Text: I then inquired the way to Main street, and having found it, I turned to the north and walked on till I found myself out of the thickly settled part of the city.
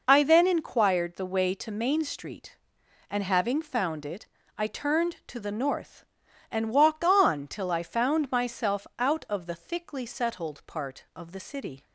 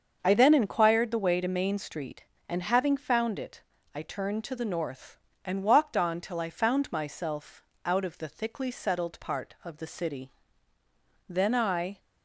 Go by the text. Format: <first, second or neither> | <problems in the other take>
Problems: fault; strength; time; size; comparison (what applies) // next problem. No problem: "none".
first | starts louder than the rest; until 1.2 s; 6.5 dB // pauses between "myself" and "out"; slight; at 7.6 s; 0.22 s long // goes on to say "Then I"; noticeable; from 11.2 s on; 0.70 s long